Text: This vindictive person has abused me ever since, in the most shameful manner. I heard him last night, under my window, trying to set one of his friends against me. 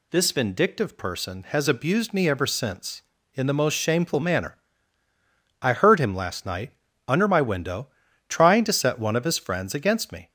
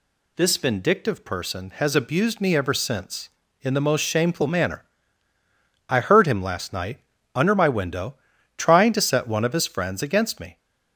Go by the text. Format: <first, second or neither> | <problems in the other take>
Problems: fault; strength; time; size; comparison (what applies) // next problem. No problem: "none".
neither | none